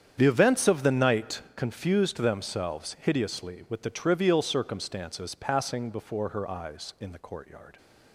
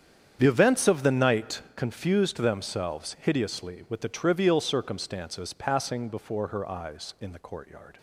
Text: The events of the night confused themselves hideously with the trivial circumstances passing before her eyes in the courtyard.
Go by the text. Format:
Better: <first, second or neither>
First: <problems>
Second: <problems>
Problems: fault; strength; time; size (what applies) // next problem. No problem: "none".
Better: neither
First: starts louder than the rest; strong; until 1.1 s; 8.5 dB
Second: starts louder than the rest; strong; until 1.4 s; 8.5 dB